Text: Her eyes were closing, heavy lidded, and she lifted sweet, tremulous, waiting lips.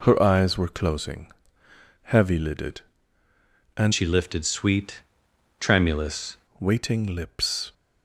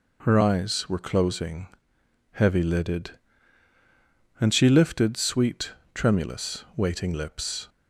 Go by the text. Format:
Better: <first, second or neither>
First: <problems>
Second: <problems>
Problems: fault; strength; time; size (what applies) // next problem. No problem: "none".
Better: second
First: changes voice from "she" to "tremulous"; from 3.9 to 6.3 s; 2.4 s long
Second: none